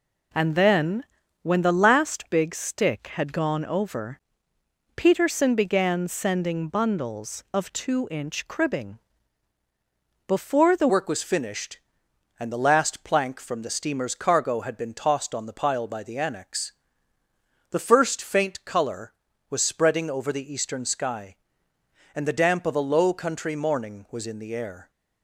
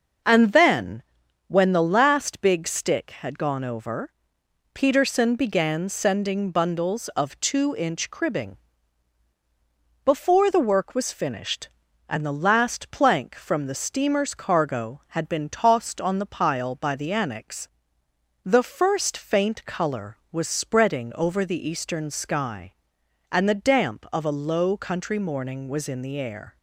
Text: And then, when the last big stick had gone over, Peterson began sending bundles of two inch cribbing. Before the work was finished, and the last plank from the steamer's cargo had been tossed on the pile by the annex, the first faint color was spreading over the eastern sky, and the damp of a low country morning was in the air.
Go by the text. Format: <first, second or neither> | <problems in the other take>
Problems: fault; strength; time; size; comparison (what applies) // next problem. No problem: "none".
second | changes voice at "work"; from 10.8 s on; 14.0 s long